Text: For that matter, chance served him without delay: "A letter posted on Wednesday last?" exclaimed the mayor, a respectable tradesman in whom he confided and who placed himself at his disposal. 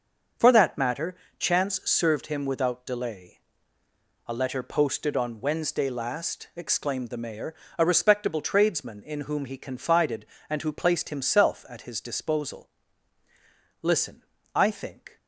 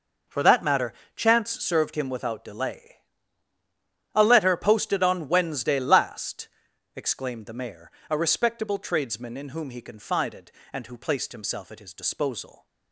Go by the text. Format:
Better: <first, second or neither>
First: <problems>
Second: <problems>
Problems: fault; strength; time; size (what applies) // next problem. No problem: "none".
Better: second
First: starts louder than the rest; until 1.6 s; 6.5 dB // goes on to say "Listen I think"; from 13.8 s on; 1.3 s long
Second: none